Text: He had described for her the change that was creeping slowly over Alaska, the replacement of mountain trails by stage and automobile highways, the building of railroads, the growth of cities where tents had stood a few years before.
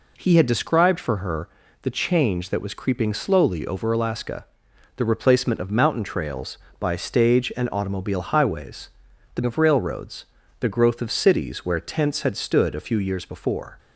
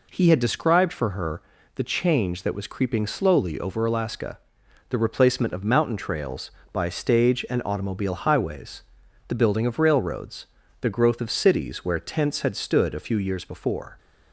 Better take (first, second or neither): second